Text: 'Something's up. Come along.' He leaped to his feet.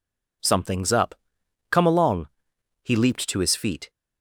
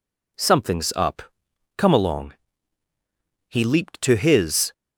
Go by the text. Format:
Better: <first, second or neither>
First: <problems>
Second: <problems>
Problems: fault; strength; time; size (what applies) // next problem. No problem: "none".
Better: first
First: none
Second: stops before "feet"; at 4.7 s